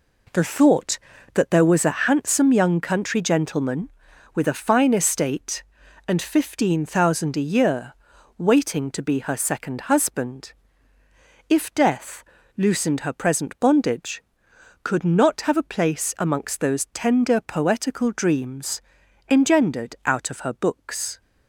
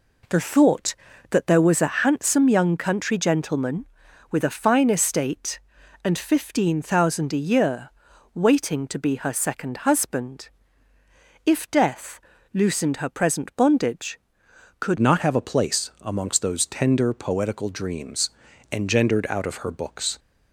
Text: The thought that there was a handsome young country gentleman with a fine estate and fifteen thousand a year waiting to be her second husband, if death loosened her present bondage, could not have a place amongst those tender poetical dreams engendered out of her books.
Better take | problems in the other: first | pauses between "year" and "waiting"; at 7.9 s; 0.44 s long; also in the first // pauses between "death" and "loosened"; slight; at 12.2 s; 0.34 s long; slight in the first // changes voice at "not"; from 14.9 s on; 5.2 s long // pauses between "dreams" and "engendered"; at 18.2 s; 0.42 s long; noticeable in the first

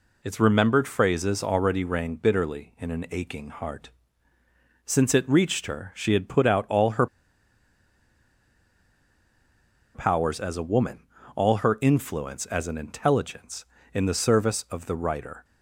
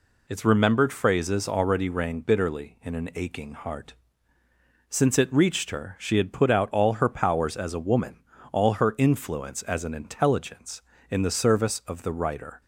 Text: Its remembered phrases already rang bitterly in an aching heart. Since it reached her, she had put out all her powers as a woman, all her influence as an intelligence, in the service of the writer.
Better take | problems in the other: second | pauses between "her" and "powers"; strong; at 7.0 s; 2.8 s long

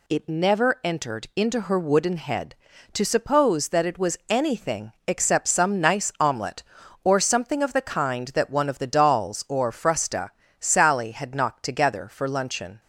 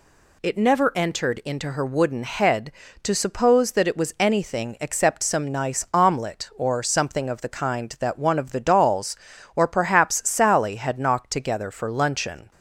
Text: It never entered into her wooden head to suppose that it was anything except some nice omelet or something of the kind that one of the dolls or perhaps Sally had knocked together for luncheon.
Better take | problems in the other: second | pauses between "anything" and "except"; slight; at 4.9 s; 0.16 s long // says "frusta" for "perhaps"; at 9.7 s

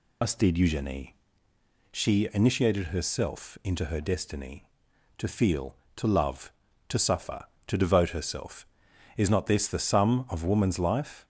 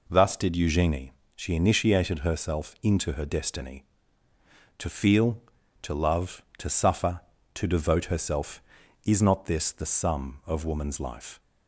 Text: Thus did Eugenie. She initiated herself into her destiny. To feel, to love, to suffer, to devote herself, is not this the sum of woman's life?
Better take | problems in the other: second | loses the start of "Thus"; at 0.2 s; 110 ms

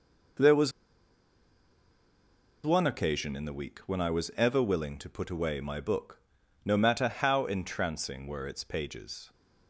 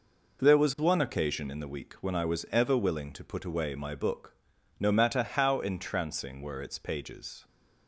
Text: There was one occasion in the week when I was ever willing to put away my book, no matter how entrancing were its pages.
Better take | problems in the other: second | pauses between "was" and "one"; strong; at 0.7 s; 1.9 s long

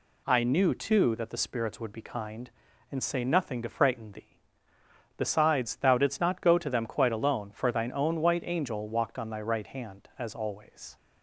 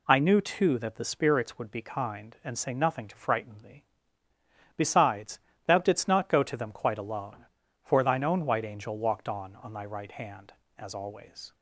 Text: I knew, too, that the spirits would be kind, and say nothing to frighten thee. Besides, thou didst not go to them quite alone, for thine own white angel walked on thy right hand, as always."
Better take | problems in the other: first | says "on" twice; at 9.5 s

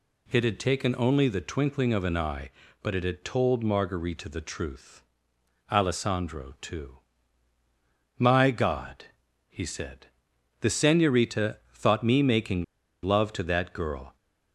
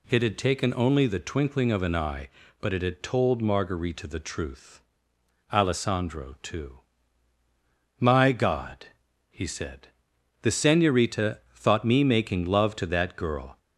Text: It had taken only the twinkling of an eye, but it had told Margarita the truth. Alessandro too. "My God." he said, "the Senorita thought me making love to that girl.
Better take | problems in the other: second | pauses between "making" and "love"; at 12.6 s; 0.38 s long

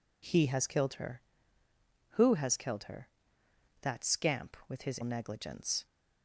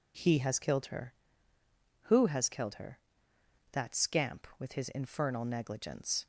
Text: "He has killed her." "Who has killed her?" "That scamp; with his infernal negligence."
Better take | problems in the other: second | skips "infernal"; at 5.0 s

